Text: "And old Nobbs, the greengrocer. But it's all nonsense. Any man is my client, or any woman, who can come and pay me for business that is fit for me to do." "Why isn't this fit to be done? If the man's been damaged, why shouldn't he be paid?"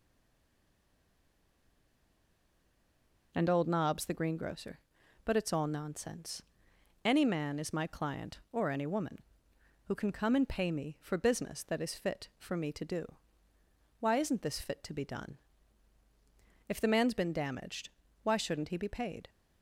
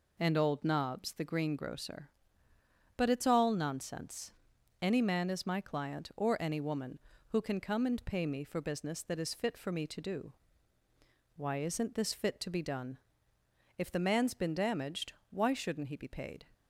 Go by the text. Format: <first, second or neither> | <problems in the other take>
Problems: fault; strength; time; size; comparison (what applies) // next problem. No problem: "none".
second | stays silent before the first word; strong; until 3.3 s; 3.3 s long